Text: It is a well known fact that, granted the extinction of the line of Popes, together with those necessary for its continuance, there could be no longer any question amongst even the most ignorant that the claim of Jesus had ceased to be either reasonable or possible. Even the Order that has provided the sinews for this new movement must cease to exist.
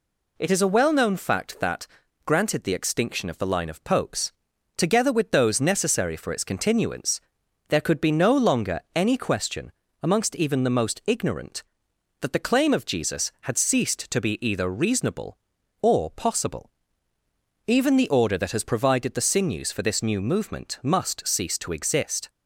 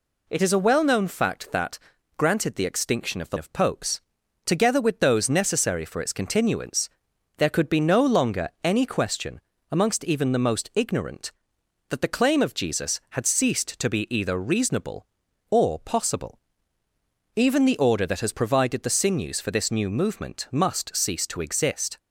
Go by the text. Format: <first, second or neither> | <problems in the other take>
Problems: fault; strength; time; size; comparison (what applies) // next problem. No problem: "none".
first | skips "line"; at 3.3 s // pauses between "longer" and "any"; slight; at 8.4 s; 0.16 s long; slight in the first // pauses between "question" and "amongst"; slight; at 9.3 s; 0.30 s long; slight in the first